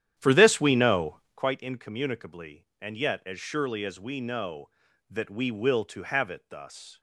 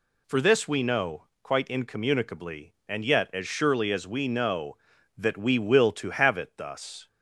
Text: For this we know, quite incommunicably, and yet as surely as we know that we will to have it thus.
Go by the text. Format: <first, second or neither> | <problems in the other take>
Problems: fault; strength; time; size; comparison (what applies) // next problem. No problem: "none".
second | starts louder than the rest; strong; until 1.6 s; 10.5 dB